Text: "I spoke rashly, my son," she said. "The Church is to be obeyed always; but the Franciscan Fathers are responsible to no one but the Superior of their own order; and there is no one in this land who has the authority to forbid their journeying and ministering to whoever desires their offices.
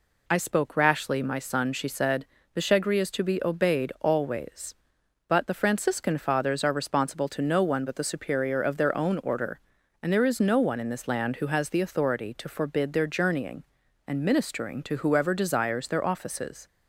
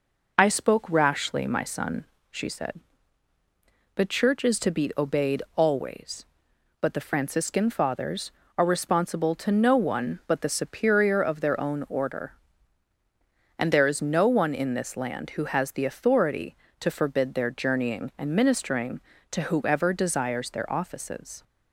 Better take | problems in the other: second | says "Shegri" for "Church"; at 2.5 s

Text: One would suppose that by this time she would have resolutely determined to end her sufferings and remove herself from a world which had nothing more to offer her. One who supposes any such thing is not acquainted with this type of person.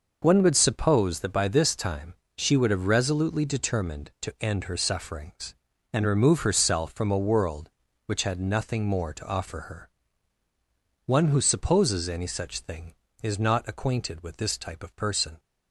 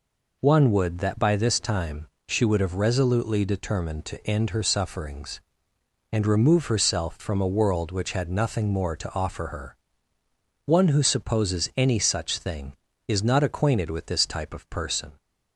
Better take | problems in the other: first | skips "suppose"; at 0.9 s // pauses between "time" and "she"; slight; at 2.0 s; 0.18 s long; slight in the first

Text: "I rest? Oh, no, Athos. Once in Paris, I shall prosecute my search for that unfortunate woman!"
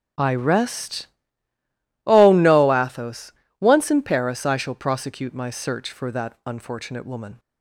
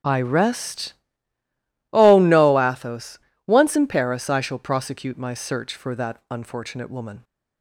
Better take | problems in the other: neither | starts louder than the rest; strong; the same in both

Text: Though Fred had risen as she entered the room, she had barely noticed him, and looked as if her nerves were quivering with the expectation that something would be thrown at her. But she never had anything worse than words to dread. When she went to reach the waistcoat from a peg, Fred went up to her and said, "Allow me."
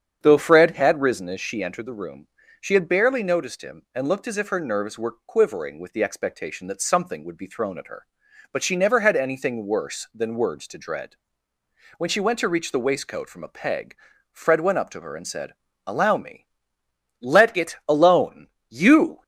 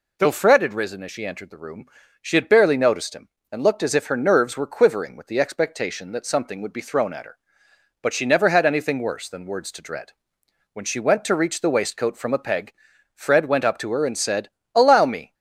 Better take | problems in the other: second | starts louder than the rest; strong; until 1.2 s; 7.5 dB // goes on to say "Let it alone You"; strong; from 17.2 s on; 2.0 s long

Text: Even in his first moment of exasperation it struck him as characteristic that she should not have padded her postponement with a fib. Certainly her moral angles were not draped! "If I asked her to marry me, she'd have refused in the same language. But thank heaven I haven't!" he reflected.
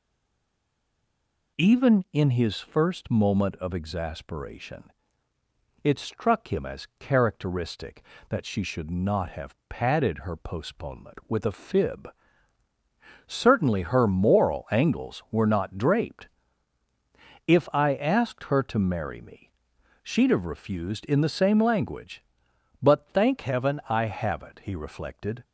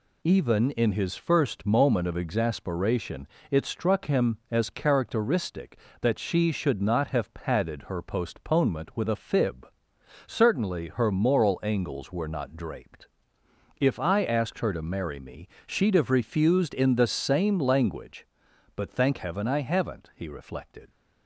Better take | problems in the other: second | stays silent before the first word; noticeable; until 1.5 s; 1.5 s long // pauses between "exasperation" and "it"; noticeable; at 4.8 s; 0.94 s long; slight in the second

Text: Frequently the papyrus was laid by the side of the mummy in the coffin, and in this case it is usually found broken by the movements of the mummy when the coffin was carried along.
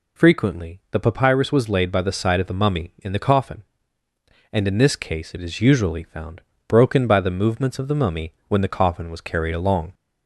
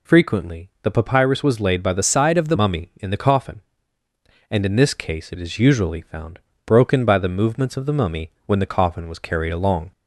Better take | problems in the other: first | changes voice from "side" to "the"; from 2.0 to 2.5 s; 0.5 s long // pauses between "found" and "broken"; slight; at 6.3 s; 0.28 s long; slight in the first // pauses between "mummy" and "when"; slight; at 8.2 s; 0.16 s long; slight in the first

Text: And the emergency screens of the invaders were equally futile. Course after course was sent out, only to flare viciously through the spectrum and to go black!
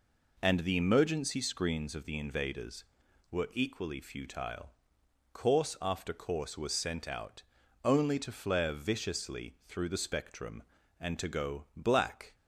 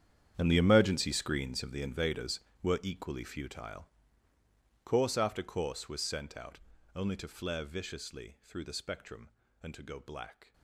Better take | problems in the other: first | gets quieter; strong; throughout; 16 dB

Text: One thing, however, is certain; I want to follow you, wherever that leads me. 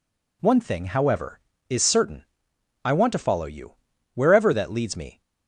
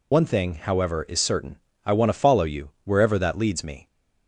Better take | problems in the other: first | loses the start of "One"; at 0.1 s; 70 ms

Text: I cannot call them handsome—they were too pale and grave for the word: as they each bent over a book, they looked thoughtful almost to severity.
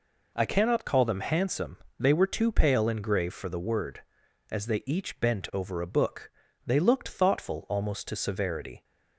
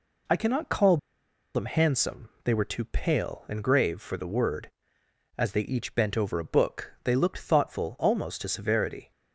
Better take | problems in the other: first | pauses between "call" and "them"; noticeable; at 0.9 s; 0.57 s long

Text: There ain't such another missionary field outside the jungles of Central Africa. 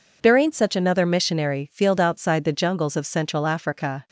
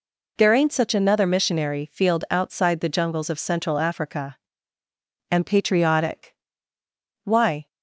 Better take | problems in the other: first | goes on to say "And patriotic why"; strong; from 5.2 s on; 2.3 s long

